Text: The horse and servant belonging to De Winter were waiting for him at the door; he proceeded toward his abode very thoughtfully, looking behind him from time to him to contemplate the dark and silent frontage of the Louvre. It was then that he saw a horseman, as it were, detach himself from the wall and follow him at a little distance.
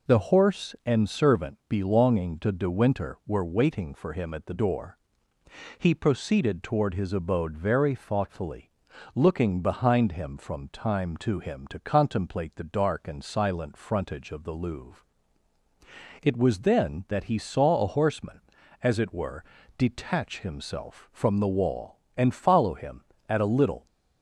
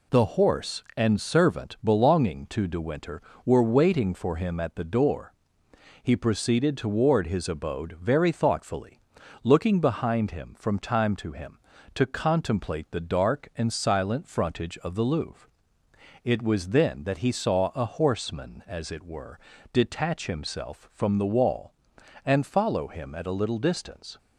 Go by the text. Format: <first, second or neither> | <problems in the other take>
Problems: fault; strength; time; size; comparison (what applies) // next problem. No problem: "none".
second | stops before "distance"; at 23.8 s